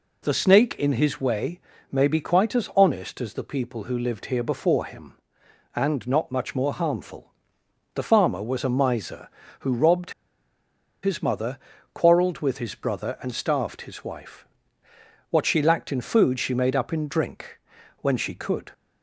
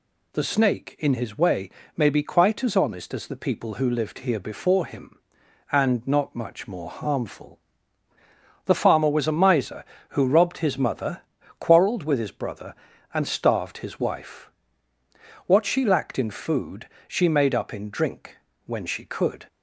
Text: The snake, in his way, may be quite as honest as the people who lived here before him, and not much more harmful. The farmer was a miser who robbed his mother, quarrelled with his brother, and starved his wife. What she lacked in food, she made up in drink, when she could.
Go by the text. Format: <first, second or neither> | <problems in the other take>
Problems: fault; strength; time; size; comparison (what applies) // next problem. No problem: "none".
second | pauses between "robbed" and "his"; noticeable; at 10.1 s; 0.91 s long